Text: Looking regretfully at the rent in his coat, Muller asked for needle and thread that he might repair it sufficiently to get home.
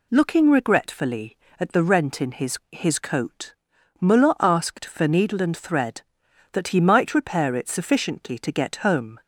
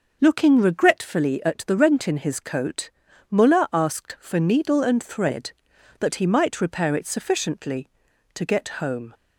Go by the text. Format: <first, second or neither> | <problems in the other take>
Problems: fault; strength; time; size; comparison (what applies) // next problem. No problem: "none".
second | says "his" twice; at 2.7 s